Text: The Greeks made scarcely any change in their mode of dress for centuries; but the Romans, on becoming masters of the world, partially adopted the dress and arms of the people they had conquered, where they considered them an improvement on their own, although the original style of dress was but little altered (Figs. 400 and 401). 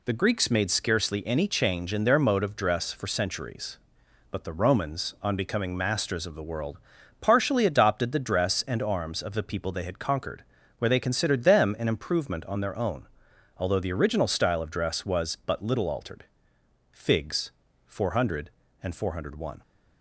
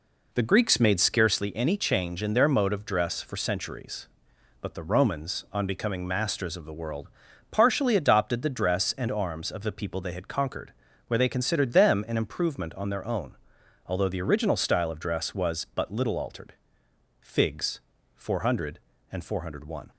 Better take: first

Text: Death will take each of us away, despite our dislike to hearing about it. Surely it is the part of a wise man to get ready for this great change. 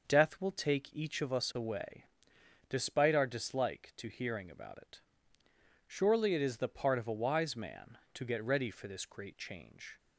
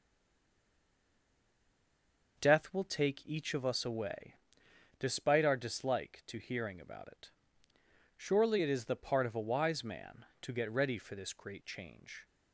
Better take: first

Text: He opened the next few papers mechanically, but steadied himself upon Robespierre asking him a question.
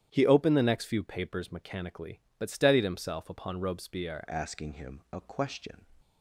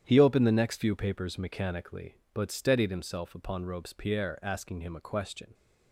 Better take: second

